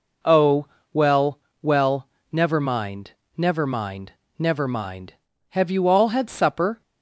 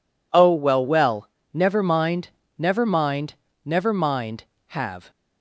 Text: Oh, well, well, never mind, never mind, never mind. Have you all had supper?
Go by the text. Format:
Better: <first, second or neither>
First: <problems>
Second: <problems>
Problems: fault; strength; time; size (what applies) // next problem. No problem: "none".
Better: first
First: none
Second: stops before "you all had supper"; at 5.0 s